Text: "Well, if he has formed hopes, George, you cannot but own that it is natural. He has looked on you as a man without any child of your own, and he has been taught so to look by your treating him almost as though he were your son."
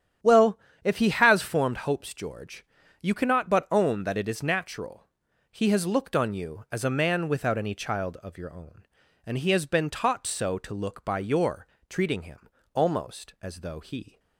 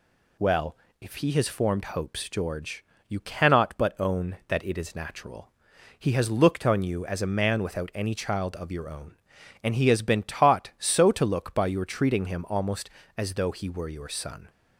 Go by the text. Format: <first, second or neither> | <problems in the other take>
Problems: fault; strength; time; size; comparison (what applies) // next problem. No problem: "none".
second | starts louder than the rest; strong; until 1.4 s; 9.5 dB // pauses between "your" and "treating"; slight; at 11.6 s; 0.22 s long // pauses between "him" and "almost"; slight; at 12.4 s; 0.24 s long // stops before "were your son"; at 14.1 s